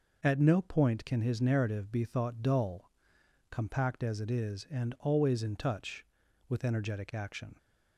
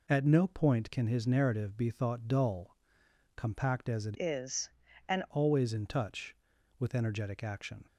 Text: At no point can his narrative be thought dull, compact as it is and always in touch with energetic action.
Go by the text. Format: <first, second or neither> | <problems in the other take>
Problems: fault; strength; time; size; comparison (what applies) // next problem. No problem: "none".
first | changes voice from "is" to "and"; from 4.1 to 5.2 s; 1.1 s long